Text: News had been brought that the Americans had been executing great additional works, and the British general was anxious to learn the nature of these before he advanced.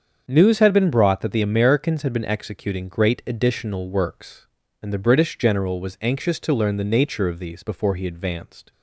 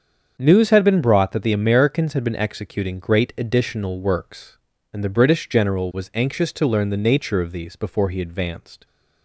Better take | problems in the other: neither | starts louder than the rest; the same in both

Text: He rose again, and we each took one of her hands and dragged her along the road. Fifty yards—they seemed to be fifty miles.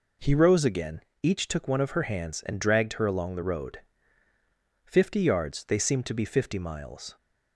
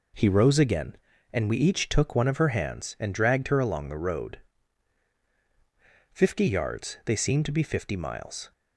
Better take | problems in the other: second | skips "and we"; at 1.1 s

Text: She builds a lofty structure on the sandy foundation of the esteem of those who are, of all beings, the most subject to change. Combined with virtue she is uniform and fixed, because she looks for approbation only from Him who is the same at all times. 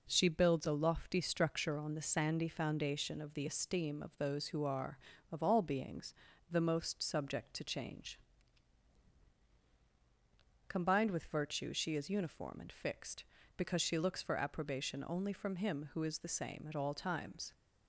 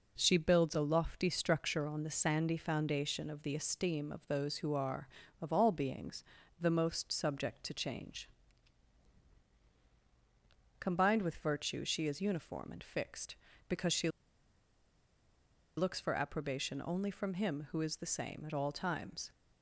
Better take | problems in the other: first | pauses between "she" and "looks"; strong; at 14.0 s; 1.6 s long

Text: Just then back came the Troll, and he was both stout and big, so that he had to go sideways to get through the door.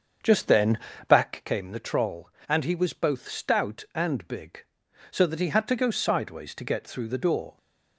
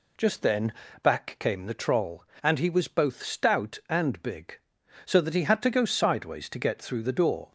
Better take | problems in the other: second | starts louder than the rest; until 1.5 s; 7 dB // pauses between "then" and "back"; slight; at 0.7 s; 0.30 s long; slight in the second

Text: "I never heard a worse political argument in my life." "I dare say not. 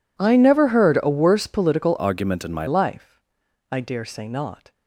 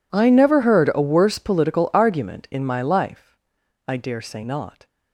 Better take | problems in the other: second | changes voice from "argument" to "my"; from 1.9 to 2.6 s; 0.7 s long

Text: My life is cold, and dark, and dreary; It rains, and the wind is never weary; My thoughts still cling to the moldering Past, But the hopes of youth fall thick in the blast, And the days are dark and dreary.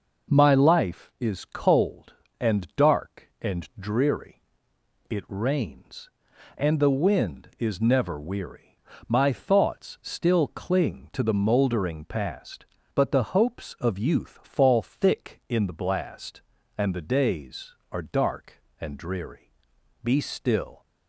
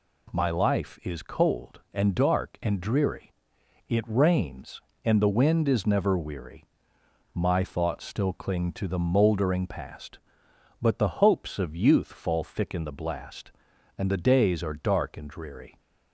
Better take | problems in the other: second | goes on to say "Be still"; noticeable; from 20.0 s on; 0.82 s long

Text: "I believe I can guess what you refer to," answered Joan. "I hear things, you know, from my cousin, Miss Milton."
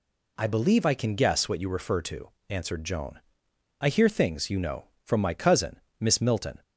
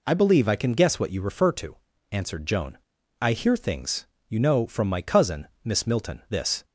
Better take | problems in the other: first | goes on to say "This"; slight; from 6.2 s on; 0.36 s long

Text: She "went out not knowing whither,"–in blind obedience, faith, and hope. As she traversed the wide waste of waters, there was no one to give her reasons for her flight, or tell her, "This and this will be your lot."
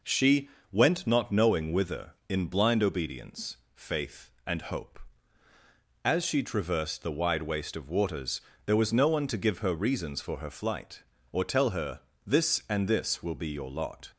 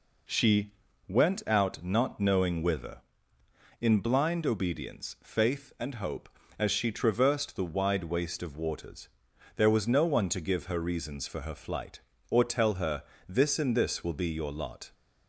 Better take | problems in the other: second | pauses between "She" and "went"; slight; at 0.4 s; 0.24 s long; slight in the second // skips "out"; at 1.0 s

